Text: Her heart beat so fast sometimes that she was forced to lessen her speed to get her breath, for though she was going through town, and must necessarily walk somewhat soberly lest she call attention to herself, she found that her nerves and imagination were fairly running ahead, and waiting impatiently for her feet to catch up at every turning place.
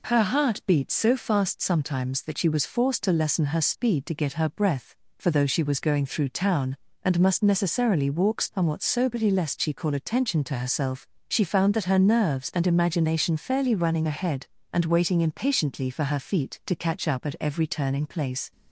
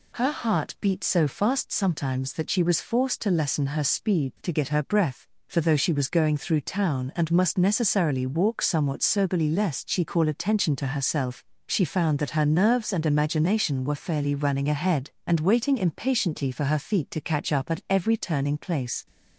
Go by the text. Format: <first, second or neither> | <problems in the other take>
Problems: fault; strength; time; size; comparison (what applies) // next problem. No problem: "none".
second | skips "were"; at 13.3 s